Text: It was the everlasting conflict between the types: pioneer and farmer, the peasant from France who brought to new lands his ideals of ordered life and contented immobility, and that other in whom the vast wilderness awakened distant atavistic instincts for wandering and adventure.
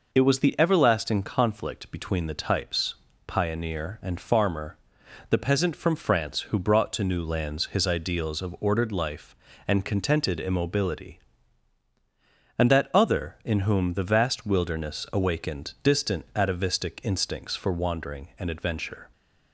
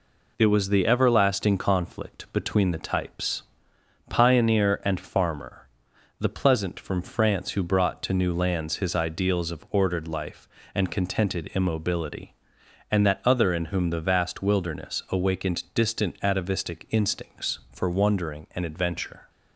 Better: first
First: none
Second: says "pleasant" for "peasant"; at 6.2 s

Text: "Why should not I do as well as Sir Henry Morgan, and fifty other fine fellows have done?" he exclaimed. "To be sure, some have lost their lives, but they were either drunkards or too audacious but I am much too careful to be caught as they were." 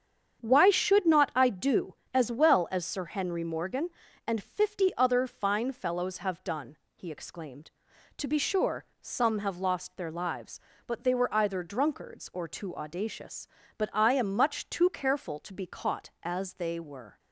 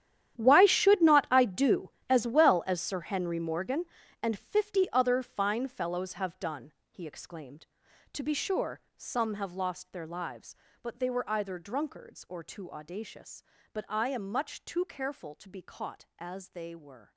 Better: first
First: starts louder than the rest; strong; until 1.4 s; 8 dB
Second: gets quieter; strong; throughout; 17 dB // starts louder than the rest; strong; until 1.4 s; 11 dB

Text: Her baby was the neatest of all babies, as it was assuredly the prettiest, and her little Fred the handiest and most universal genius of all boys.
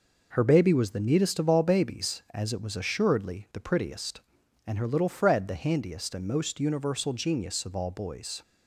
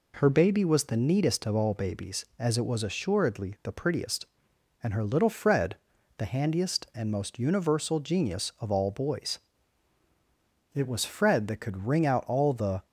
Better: first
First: none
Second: pauses between "Fred" and "the"; at 5.7 s; 0.42 s long // goes on to say "It was Fred that could wring out all the"; strong; from 10.7 s on; 2.1 s long

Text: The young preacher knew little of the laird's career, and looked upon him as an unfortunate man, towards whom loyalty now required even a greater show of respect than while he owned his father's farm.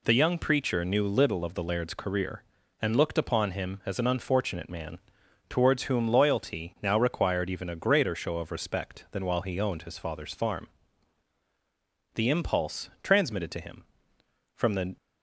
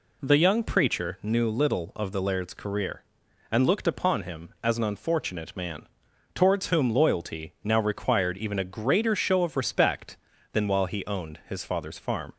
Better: second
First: goes on to say "The impulse transmitted to him from the"; strong; from 12.1 s on; 2.8 s long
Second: none

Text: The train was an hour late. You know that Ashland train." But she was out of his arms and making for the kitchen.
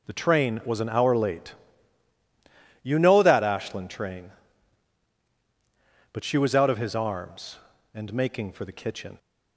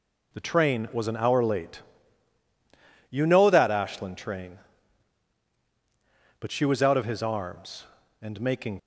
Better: first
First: none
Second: stops before "for the kitchen"; at 8.7 s

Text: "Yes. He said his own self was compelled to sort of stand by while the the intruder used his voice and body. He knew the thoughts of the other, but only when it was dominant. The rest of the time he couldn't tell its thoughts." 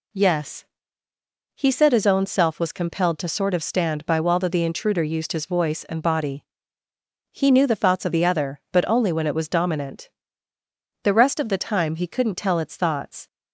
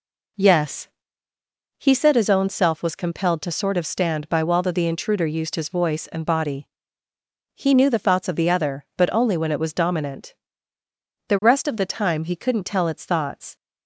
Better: first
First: none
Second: starts louder than the rest; until 2.0 s; 4 dB

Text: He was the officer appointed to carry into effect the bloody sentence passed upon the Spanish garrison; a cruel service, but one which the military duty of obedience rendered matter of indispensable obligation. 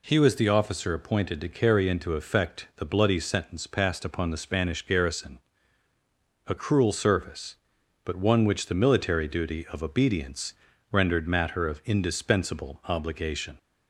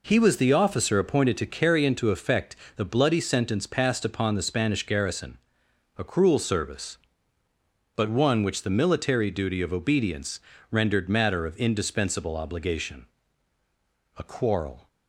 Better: first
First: pauses between "obedience" and "rendered"; at 10.5 s; 0.38 s long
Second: pauses between "effect" and "the"; slight; at 2.5 s; 0.20 s long // pauses between "obedience" and "rendered"; slight; at 10.3 s; 0.30 s long // goes on to say "A quarrel"; noticeable; from 14.1 s on; 0.70 s long

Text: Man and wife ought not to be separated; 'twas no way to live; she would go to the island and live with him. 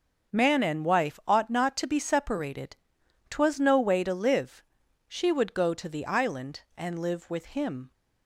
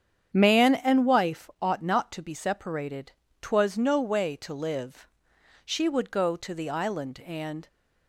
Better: first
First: starts louder than the rest; until 1.4 s; 6.5 dB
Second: starts louder than the rest; strong; until 1.3 s; 8.5 dB // stops before "live with him"; at 7.6 s

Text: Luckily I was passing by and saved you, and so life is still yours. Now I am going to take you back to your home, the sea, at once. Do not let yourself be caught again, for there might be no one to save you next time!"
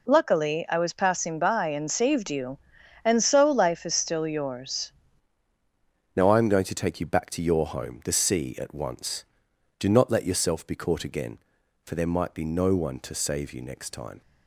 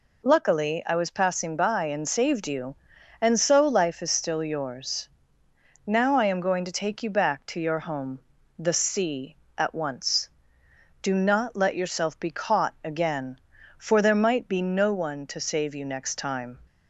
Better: second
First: changes voice at "Now"; from 6.1 s on; 8.1 s long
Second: none

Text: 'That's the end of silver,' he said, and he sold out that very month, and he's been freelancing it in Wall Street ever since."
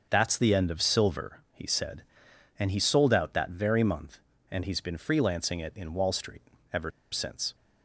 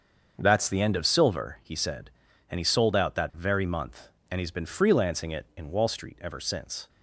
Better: second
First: starts louder than the rest; until 1.1 s; 6.5 dB // pauses between "Street" and "ever"; slight; at 6.4 s; 0.30 s long // pauses between "ever" and "since"; slight; at 6.9 s; 0.22 s long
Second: starts louder than the rest; until 1.3 s; 6.5 dB

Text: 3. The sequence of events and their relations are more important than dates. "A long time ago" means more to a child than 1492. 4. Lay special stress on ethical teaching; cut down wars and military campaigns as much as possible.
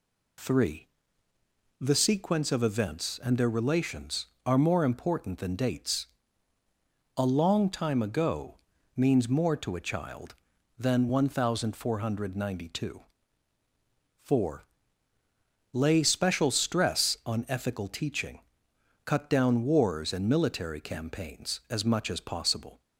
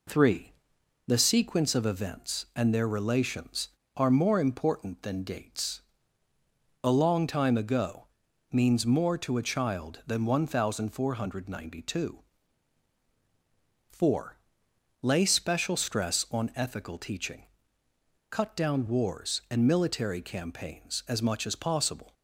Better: neither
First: pauses between "ago" and "means"; at 8.5 s; 0.40 s long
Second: pauses between "ago" and "means"; at 8.0 s; 0.44 s long

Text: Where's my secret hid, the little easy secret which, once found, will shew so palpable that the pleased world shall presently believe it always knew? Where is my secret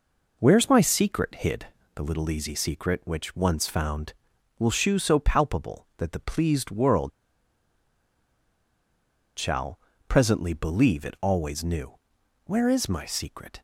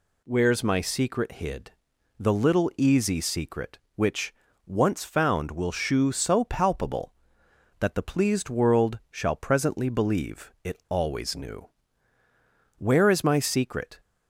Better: second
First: pauses between "world" and "shall"; strong; at 7.1 s; 2.2 s long // pauses between "shall" and "presently"; slight; at 9.7 s; 0.30 s long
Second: none

